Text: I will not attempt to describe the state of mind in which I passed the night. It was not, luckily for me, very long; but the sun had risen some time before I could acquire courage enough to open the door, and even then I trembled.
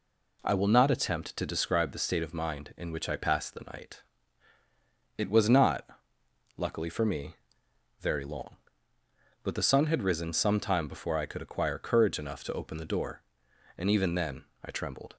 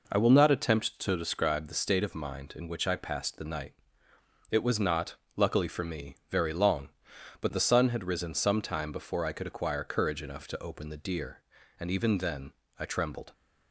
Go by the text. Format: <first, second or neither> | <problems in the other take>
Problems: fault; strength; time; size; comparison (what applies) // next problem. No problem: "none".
first | says "deer" for "door"; at 11.0 s // pauses between "then" and "I"; slight; at 12.5 s; 0.26 s long; slight in the first